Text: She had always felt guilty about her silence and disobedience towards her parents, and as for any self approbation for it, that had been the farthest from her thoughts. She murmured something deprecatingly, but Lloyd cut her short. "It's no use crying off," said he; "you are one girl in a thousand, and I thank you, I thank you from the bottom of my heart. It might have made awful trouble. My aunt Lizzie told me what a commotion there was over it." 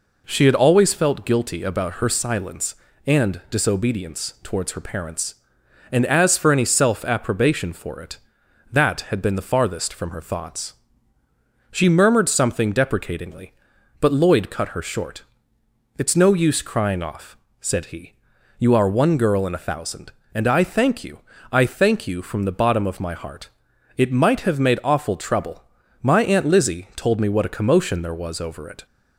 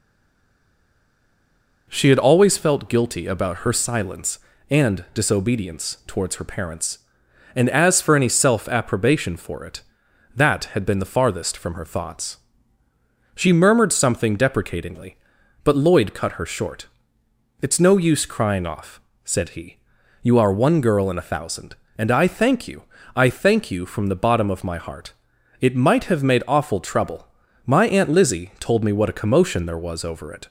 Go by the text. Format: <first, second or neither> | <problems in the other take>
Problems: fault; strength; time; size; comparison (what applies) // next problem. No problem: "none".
first | stays silent before the first word; noticeable; until 1.8 s; 1.8 s long